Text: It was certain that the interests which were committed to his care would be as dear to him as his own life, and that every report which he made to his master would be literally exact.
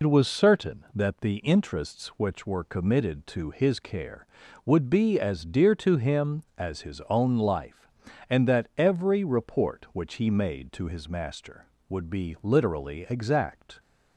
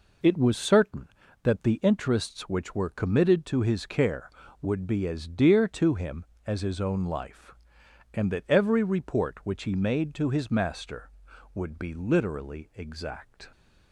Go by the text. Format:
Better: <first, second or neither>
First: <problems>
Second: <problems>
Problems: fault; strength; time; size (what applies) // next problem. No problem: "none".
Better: second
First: loses the start of "It"; at 0.0 s; 75 ms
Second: none